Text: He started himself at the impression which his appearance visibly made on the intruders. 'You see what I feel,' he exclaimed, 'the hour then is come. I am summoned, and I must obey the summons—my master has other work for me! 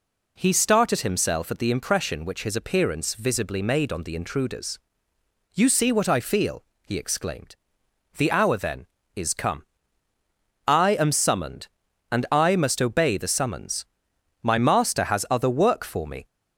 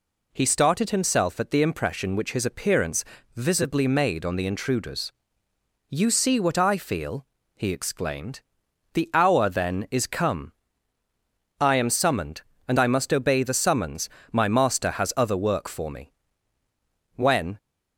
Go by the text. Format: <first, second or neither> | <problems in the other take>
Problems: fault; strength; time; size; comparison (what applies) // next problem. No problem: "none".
first | pauses between "appearance" and "visibly"; slight; at 3.0 s; 0.30 s long // goes on to say "When"; slight; from 17.1 s on; 0.42 s long